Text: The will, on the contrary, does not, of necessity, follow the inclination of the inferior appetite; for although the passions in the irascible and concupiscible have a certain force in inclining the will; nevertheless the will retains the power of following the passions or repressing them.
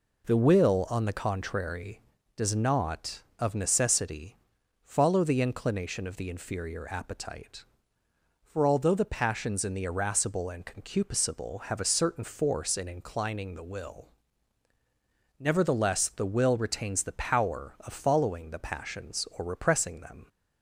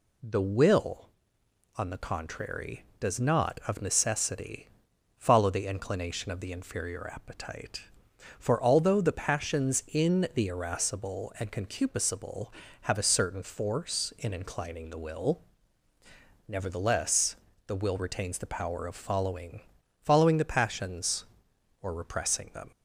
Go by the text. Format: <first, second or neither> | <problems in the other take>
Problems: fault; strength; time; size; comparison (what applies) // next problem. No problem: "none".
first | pauses between "nevertheless" and "the"; slight; at 17.3 s; 0.30 s long // says "following" twice; at 20.0 s